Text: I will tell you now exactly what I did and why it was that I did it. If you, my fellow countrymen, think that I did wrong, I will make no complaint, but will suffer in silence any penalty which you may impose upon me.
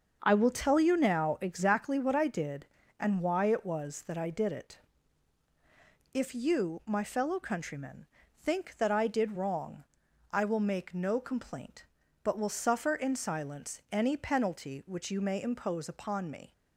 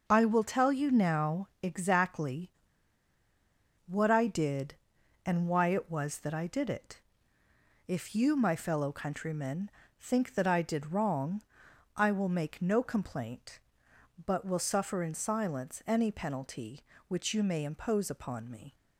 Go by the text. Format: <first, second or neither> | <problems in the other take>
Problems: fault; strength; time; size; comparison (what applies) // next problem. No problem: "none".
first | starts louder than the rest; noticeable; until 1.0 s; 6 dB; also in the first // pauses between "exactly" and "what"; strong; at 2.5 s; 1.3 s long